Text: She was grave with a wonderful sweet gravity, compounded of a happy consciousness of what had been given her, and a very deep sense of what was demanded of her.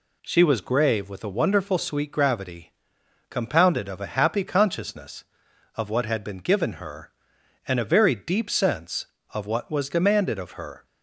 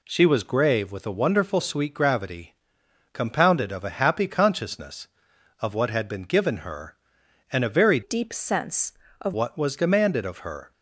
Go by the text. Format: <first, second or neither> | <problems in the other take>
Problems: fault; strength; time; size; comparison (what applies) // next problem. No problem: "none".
first | changes voice from "deep" to "of"; from 8.0 to 9.3 s; 1.3 s long